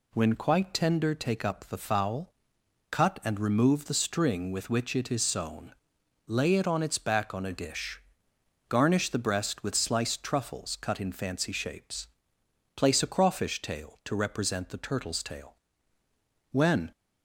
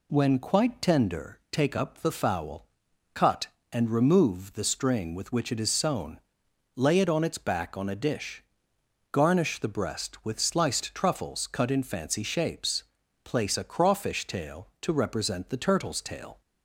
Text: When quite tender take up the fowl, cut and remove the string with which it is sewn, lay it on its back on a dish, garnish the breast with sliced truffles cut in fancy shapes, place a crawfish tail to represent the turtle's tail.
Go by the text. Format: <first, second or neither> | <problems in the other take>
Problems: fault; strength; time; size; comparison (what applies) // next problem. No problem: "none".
second | goes on to say "When"; slight; from 16.5 s on; 0.40 s long